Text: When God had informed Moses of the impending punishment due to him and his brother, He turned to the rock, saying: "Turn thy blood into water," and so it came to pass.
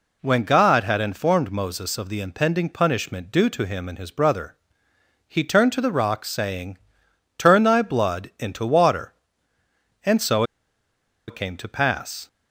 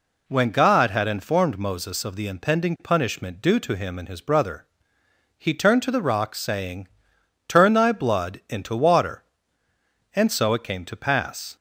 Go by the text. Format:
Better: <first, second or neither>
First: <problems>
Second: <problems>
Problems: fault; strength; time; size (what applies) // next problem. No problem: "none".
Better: second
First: pauses between "so" and "it"; noticeable; at 10.4 s; 0.84 s long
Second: none